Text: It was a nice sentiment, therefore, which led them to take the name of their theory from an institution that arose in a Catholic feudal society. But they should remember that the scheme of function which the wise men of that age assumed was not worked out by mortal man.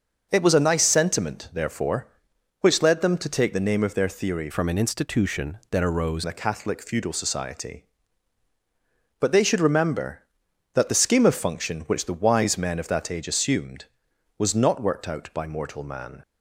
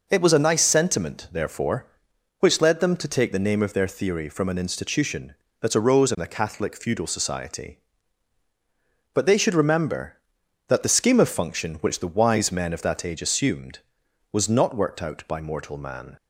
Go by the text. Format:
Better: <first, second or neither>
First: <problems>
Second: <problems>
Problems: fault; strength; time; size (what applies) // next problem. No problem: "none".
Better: second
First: starts louder than the rest; noticeable; until 1.3 s; 6 dB // changes voice from "from" to "arose"; from 4.5 to 6.2 s; 1.7 s long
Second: none